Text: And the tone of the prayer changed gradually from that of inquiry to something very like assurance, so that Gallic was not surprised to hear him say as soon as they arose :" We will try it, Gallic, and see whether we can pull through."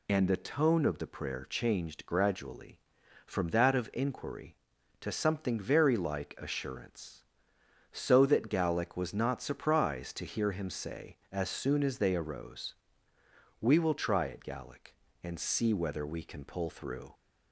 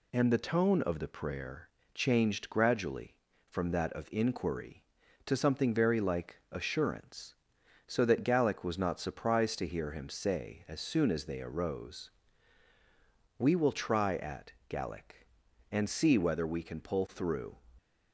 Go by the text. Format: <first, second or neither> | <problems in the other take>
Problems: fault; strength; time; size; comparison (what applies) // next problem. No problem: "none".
first | pauses between "prayer" and "changed"; slight; at 1.6 s; 0.26 s long // says "at" for "it"; at 14.1 s